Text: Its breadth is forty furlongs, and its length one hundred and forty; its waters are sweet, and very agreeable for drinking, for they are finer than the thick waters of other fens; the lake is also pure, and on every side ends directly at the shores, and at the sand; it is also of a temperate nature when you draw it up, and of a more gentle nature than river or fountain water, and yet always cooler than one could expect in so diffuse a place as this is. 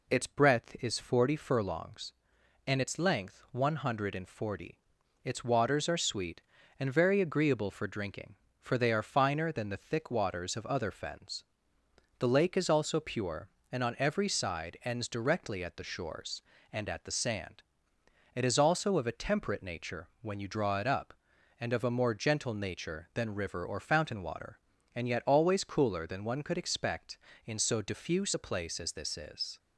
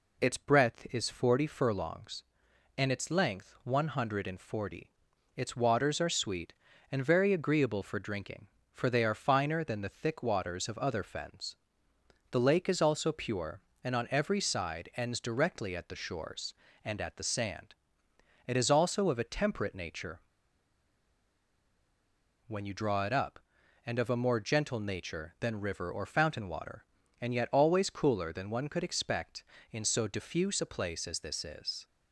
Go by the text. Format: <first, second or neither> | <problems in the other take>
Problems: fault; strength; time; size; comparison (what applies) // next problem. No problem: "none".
first | pauses between "nature" and "when"; strong; at 20.1 s; 2.2 s long